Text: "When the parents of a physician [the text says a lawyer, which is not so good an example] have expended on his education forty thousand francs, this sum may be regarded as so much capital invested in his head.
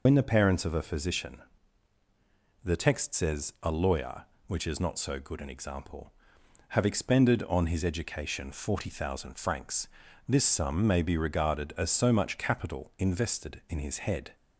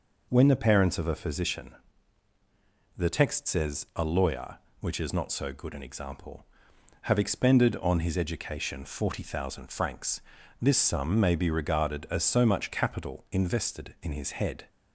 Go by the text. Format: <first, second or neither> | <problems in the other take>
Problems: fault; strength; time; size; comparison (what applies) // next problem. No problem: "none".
second | loses the start of "When"; at 0.0 s; 80 ms // pauses between "physician" and "the"; at 1.4 s; 1.2 s long; also in the second